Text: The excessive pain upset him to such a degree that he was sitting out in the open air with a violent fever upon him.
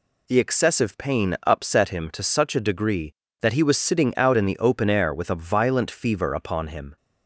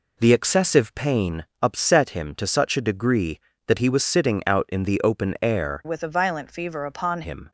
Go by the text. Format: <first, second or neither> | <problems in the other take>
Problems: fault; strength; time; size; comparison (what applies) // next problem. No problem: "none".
first | pauses between "pain" and "upset"; slight; at 1.4 s; 0.16 s long // changes voice from "with" to "upon"; from 5.8 to 7.2 s; 1.4 s long